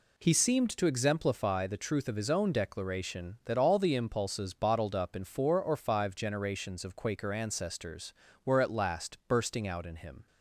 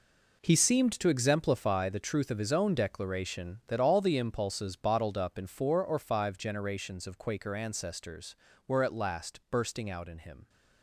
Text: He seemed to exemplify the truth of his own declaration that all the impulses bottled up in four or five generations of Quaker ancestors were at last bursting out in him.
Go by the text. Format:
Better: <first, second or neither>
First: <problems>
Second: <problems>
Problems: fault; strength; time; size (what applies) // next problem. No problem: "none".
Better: first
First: none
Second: gets quieter; strong; throughout; 11.5 dB